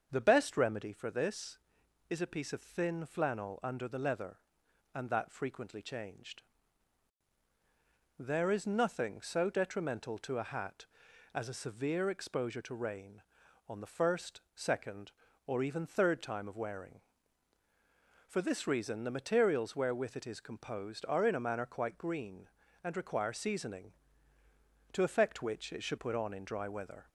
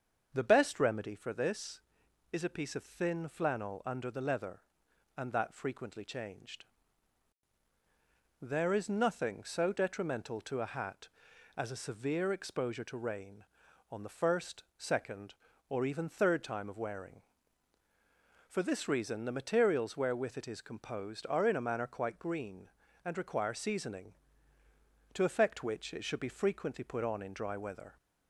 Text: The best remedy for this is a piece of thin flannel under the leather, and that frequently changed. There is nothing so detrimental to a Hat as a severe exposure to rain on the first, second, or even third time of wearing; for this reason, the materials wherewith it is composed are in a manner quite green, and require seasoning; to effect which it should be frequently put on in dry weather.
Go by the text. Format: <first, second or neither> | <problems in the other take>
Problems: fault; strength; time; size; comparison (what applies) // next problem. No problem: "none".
second | starts louder than the rest; until 1.1 s; 7 dB; also in the second // skips "be frequently"; at 25.9 s